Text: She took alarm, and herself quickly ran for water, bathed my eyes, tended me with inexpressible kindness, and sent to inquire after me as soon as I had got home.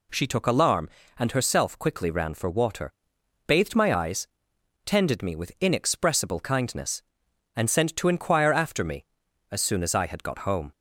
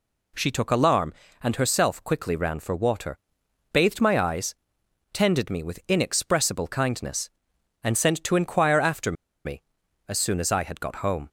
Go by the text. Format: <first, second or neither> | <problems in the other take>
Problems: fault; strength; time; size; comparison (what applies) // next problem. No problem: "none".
first | pauses between "after" and "me"; slight; at 9.1 s; 0.32 s long